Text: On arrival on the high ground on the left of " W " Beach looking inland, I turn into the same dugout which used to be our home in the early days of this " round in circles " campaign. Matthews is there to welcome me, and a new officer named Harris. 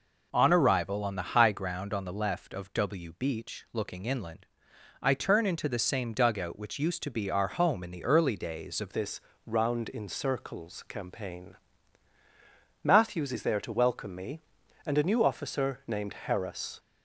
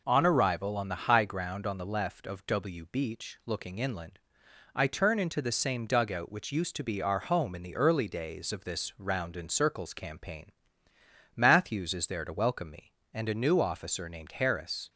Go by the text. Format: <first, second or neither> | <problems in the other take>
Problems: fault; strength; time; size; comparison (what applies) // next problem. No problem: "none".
second | changes voice at "this"; from 8.9 s on; 7.8 s long